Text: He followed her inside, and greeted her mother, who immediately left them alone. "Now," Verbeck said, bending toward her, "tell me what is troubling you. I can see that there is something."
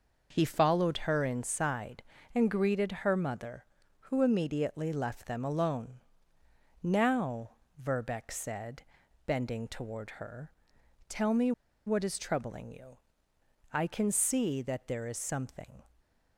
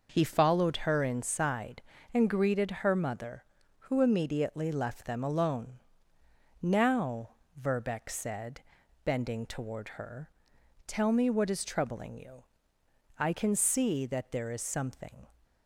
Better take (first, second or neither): second